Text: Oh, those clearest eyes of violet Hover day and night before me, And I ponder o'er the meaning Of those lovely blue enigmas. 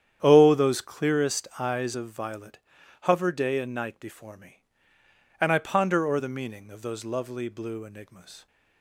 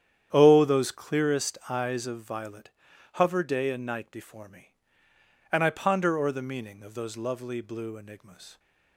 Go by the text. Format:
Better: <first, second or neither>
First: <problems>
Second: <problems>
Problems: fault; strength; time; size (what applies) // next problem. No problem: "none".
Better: neither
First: starts louder than the rest; strong; until 1.2 s; 9.5 dB // pauses between "violet" and "Hover"; at 2.5 s; 0.44 s long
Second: starts louder than the rest; strong; until 1.3 s; 9.5 dB // pauses between "violet" and "Hover"; at 2.7 s; 0.44 s long